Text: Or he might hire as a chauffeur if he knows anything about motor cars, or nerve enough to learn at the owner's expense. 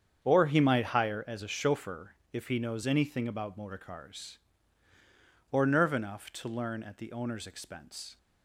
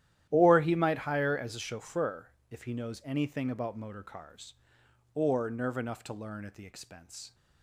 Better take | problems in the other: first | starts louder than the rest; strong; until 1.3 s; 12 dB; strong in the first // pauses between "chauffeur" and "if"; slight; at 2.3 s; 0.18 s long; slight in the first // skips "owner's"; at 6.6 s

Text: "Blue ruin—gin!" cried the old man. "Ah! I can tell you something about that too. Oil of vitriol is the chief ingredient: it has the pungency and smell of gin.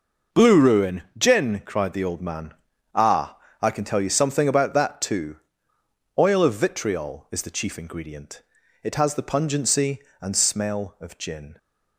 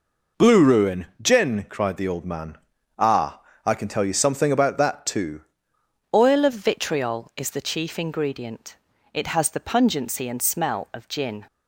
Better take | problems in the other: first | changes voice at "Oil"; from 6.1 s on; 5.3 s long

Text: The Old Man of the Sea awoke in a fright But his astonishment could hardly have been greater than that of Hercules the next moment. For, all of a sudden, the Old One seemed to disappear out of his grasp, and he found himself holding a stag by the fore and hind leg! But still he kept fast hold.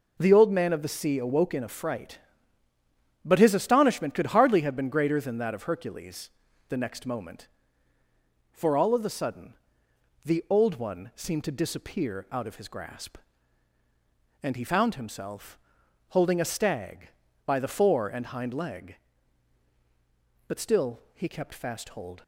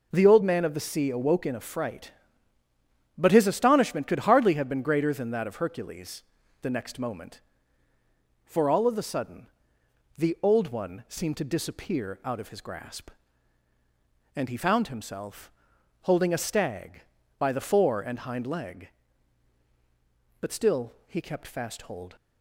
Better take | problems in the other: neither | pauses between "Hercules" and "the"; the same in both // pauses between "himself" and "holding"; noticeable; the same in both

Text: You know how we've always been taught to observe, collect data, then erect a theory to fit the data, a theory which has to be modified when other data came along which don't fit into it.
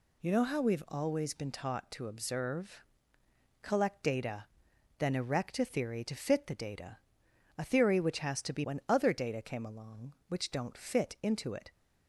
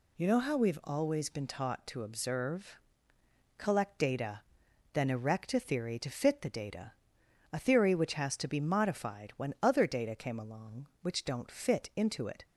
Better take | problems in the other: second | skips "modified"; at 8.6 s

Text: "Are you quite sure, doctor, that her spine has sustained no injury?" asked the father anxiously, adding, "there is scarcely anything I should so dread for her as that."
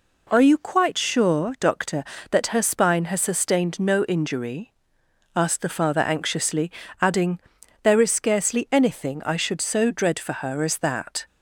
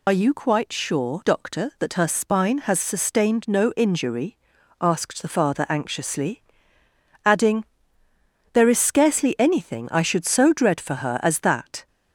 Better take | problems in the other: first | loses the start of "Are"; at 0.0 s; 35 ms

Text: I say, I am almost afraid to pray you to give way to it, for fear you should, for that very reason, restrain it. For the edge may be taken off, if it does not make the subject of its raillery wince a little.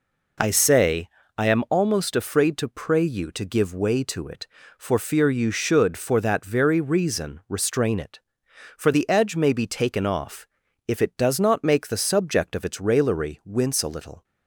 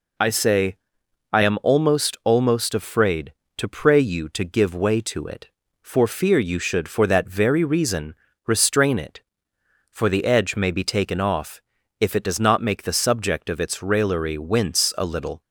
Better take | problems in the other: first | says "almost" twice; at 2.2 s

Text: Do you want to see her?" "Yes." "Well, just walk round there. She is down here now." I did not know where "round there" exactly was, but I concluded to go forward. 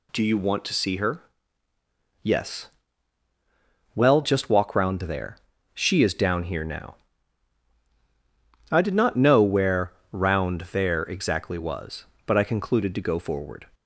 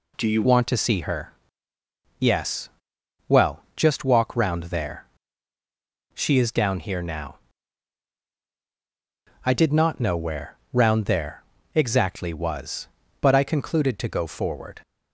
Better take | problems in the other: first | changes voice at "want"; from 0.4 s on; 14.4 s long // pauses between "where" and "round"; slight; at 10.5 s; 0.16 s long; slight in the first // pauses between "there" and "exactly"; slight; at 11.4 s; 0.30 s long

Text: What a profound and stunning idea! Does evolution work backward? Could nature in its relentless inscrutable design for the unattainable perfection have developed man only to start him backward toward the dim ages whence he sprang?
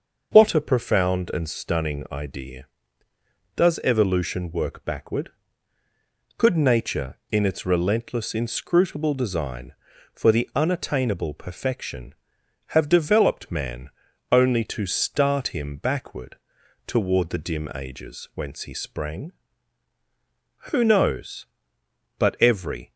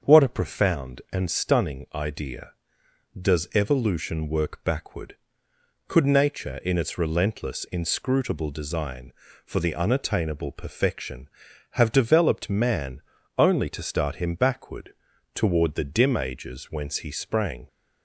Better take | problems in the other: second | starts louder than the rest; noticeable; until 1.3 s; 6 dB; also in the second // pauses between "man" and "only"; at 13.9 s; 0.40 s long; slight in the second // pauses between "backward" and "toward"; noticeable; at 16.3 s; 0.50 s long; also in the second // goes on to say "Who knows But every"; strong; from 20.7 s on; 2.2 s long

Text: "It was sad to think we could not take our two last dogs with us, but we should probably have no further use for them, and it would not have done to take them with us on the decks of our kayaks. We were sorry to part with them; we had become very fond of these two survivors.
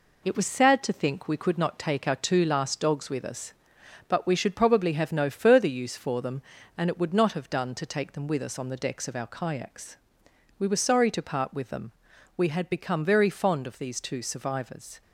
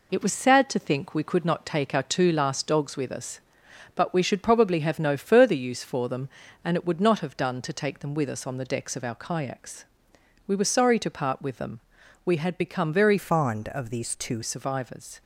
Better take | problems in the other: first | changes voice from "fond" to "two"; from 13.1 to 14.4 s; 1.3 s long

